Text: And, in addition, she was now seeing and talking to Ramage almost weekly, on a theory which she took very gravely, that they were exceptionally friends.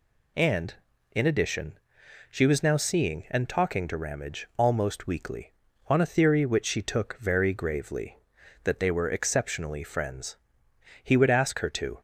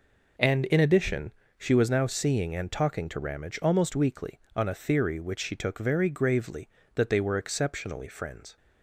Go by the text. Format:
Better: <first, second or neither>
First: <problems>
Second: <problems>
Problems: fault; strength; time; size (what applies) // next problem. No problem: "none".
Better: second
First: goes on to say "He would ask her to"; noticeable; from 11.0 s on; 0.98 s long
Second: none